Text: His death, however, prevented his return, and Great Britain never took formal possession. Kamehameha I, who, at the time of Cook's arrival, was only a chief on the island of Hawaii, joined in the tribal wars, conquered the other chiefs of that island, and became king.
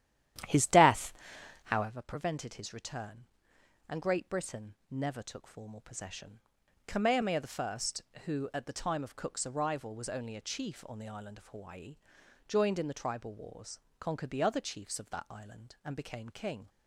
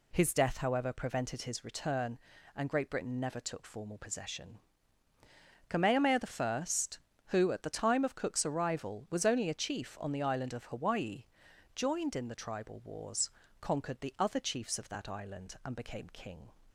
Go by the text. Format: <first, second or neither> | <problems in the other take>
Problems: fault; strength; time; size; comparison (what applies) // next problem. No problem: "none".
second | starts louder than the rest; strong; until 1.9 s; 11.5 dB // pauses between "Britain" and "never"; slight; at 4.7 s; 0.16 s long // pauses between "Kamehameha" and "I"; slight; at 7.4 s; 0.18 s long; slight in the second